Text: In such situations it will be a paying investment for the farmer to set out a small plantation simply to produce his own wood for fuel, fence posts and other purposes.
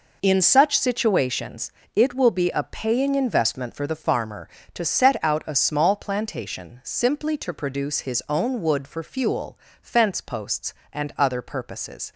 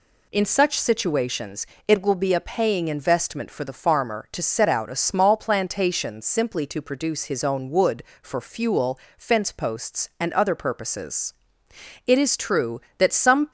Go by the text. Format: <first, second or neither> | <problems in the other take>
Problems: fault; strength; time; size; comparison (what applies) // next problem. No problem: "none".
first | pauses between "situations" and "it"; slight; at 1.6 s; 0.22 s long; slight in the first // goes on to say "It is true that some"; from 12.0 s on; 1.4 s long